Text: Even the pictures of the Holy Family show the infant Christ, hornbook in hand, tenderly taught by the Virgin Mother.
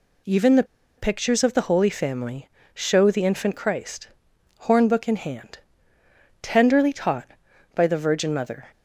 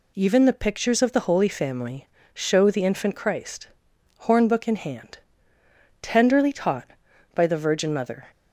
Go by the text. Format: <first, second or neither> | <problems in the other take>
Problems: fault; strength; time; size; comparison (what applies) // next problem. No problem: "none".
second | pauses between "the" and "pictures"; slight; at 0.6 s; 0.33 s long // pauses between "Family" and "show"; slight; at 2.4 s; 0.26 s long; slight in the second